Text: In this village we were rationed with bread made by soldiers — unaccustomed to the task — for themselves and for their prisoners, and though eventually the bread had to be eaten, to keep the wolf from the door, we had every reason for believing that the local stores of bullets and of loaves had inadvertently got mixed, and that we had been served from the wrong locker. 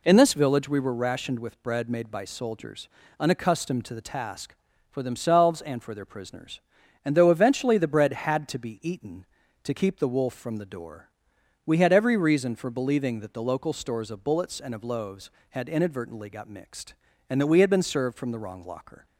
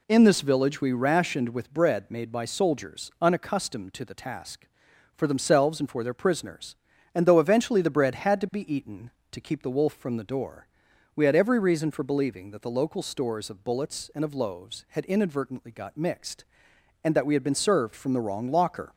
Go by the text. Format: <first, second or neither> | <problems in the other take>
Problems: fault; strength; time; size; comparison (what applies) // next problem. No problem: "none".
first | skips "were"; at 0.9 s